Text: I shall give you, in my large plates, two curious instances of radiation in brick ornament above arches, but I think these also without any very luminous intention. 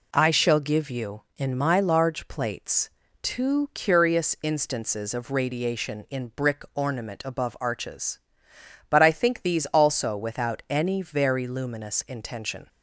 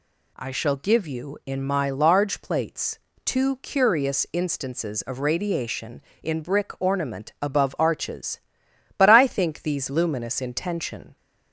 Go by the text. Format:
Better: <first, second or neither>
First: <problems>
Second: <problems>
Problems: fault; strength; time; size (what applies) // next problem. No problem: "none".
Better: first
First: none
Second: skips "also without any very"; at 9.8 s